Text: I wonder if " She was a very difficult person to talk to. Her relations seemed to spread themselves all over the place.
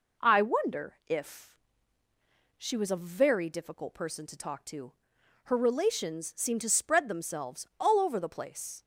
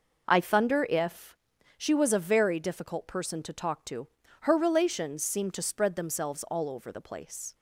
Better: first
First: none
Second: says "thunder" for "wonder"; at 0.4 s

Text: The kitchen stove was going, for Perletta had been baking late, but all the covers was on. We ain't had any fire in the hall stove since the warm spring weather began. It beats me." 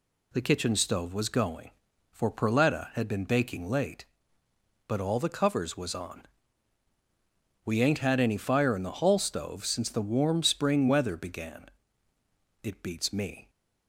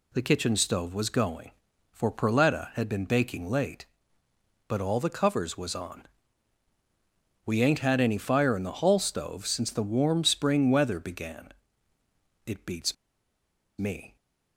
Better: first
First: none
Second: pauses between "beats" and "me"; noticeable; at 12.9 s; 0.83 s long

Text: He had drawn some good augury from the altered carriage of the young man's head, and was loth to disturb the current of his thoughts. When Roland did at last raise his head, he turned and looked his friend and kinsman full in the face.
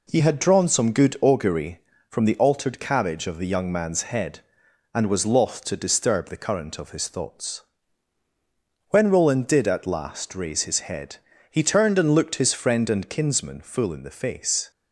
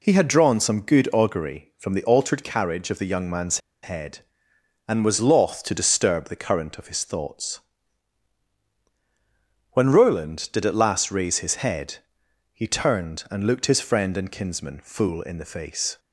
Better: first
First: none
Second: pauses between "man's" and "head"; slight; at 3.5 s; 0.24 s long

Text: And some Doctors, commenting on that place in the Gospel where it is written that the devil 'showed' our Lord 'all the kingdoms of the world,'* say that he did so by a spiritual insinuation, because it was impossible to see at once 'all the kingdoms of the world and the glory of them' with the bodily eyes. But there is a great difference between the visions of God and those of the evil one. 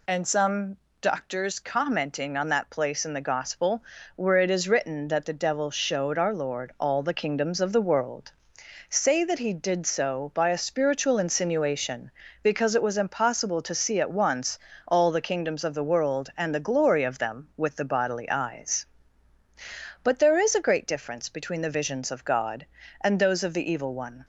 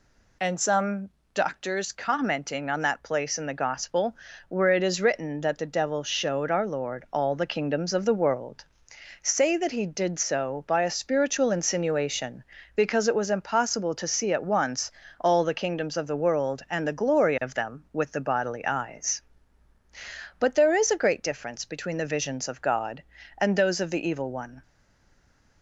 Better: first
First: pauses between "some" and "Doctors"; slight; at 0.7 s; 0.22 s long // pauses between "Gospel" and "where"; slight; at 3.8 s; 0.32 s long // pauses between "once" and "all"; slight; at 14.5 s; 0.30 s long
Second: pauses between "some" and "Doctors"; slight; at 1.1 s; 0.22 s long // pauses between "Gospel" and "where"; slight; at 4.1 s; 0.32 s long // pauses between "once" and "all"; slight; at 14.9 s; 0.30 s long // stays silent after the last word; from 24.6 s on; 1.0 s long

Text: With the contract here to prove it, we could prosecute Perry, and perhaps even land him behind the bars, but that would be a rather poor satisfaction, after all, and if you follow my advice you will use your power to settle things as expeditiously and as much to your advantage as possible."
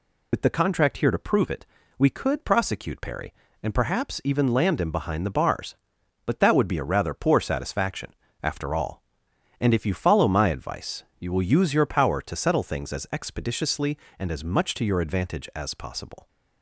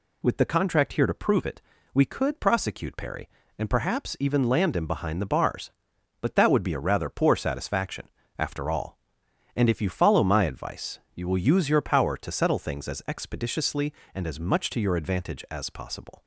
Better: second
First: loses the start of "With"; at 0.3 s; 60 ms // pauses between "advice" and "you"; slight; at 11.0 s; 0.16 s long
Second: pauses between "advice" and "you"; slight; at 10.9 s; 0.16 s long

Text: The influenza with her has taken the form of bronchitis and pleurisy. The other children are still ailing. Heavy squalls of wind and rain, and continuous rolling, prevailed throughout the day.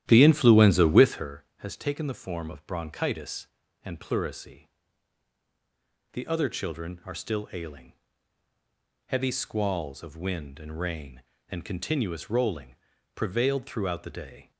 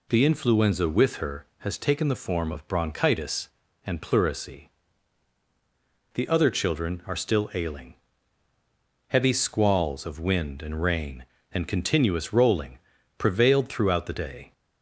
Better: second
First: starts louder than the rest; strong; until 1.3 s; 12.5 dB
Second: none

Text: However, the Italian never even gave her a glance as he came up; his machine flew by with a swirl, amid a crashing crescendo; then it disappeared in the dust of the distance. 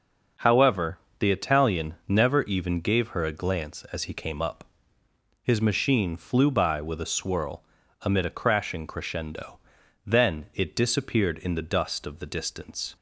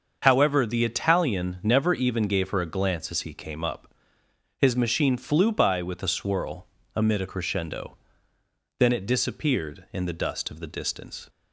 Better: first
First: none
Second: starts louder than the rest; until 1.2 s; 6.5 dB // skips "crashing"; at 7.2 s

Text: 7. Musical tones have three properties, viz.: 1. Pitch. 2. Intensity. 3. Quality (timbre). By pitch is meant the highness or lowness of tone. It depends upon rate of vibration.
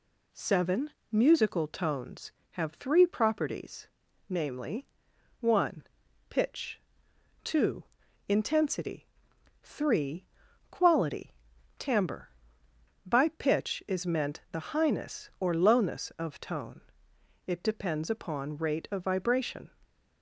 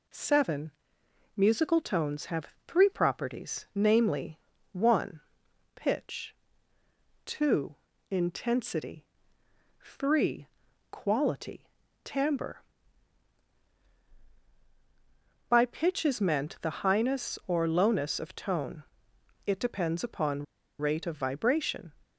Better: first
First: none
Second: pauses between "have" and "three"; slight; at 2.4 s; 0.18 s long // pauses between "upon" and "rate"; slight; at 20.4 s; 0.35 s long

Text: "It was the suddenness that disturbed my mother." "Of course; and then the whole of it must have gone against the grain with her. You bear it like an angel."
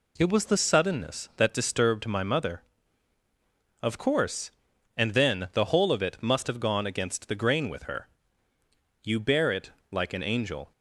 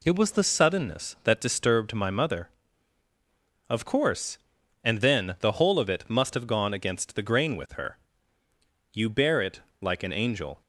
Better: neither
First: pauses between "it" and "like"; slight; at 9.7 s; 0.20 s long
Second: pauses between "it" and "like"; slight; at 9.6 s; 0.20 s long

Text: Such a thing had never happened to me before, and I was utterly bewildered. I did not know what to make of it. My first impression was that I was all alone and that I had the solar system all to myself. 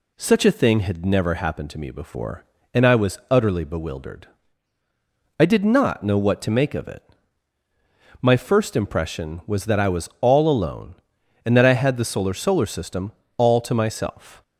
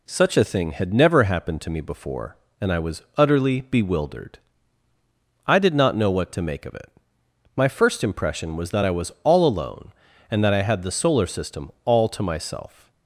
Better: second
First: says "solar" twice; at 12.3 s // pauses between "system" and "all"; slight; at 13.1 s; 0.24 s long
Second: pauses between "system" and "all"; slight; at 11.7 s; 0.16 s long

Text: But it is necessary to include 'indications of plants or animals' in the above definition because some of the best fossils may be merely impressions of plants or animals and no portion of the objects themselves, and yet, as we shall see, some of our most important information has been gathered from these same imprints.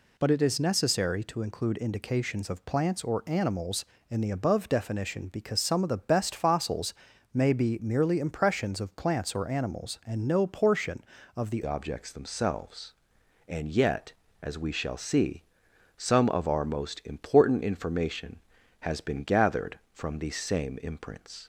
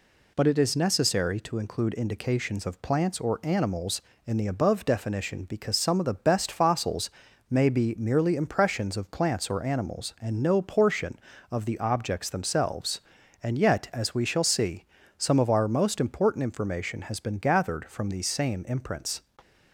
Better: second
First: pauses between "fossils" and "may"; at 6.9 s; 0.38 s long // changes voice at "objects"; from 11.6 s on; 9.8 s long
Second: pauses between "fossils" and "may"; at 7.1 s; 0.38 s long

